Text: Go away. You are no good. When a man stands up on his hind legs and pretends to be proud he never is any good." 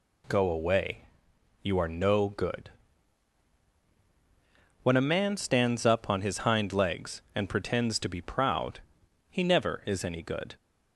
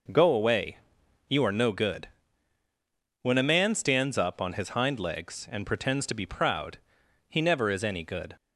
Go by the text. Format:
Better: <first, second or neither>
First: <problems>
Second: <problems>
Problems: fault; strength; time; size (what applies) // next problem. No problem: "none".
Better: neither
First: pauses between "proud" and "he"; noticeable; at 8.7 s; 0.50 s long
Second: pauses between "proud" and "he"; noticeable; at 6.7 s; 0.50 s long